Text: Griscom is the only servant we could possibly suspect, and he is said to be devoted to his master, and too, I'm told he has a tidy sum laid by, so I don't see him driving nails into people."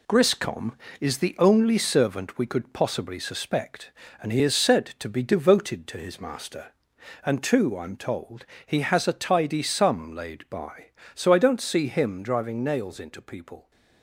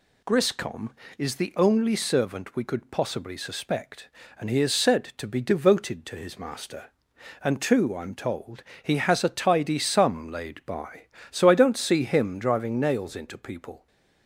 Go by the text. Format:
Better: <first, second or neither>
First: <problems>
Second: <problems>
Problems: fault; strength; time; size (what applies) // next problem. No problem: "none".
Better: second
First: gets quieter; noticeable; throughout; 6 dB // pauses between "told" and "he"; slight; at 8.4 s; 0.22 s long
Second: pauses between "told" and "he"; slight; at 8.6 s; 0.20 s long